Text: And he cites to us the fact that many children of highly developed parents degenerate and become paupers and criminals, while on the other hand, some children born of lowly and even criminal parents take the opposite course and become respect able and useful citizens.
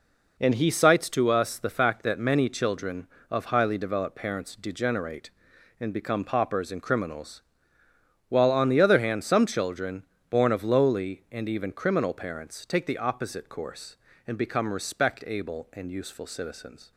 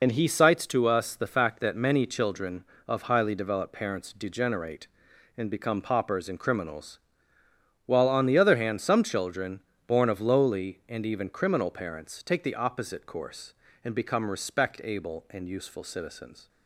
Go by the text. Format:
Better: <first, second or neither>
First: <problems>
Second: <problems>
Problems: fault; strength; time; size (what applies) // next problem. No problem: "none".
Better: first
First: pauses between "children" and "born"; slight; at 10.0 s; 0.26 s long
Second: loses the start of "And"; at 0.0 s; 55 ms // pauses between "children" and "born"; slight; at 9.6 s; 0.26 s long